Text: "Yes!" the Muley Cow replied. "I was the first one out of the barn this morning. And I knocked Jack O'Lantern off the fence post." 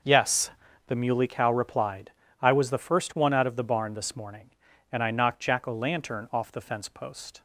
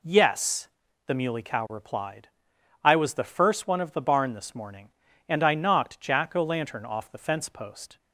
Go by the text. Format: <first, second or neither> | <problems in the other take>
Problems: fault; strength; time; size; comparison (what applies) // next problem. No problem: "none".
first | skips "out"; at 3.7 s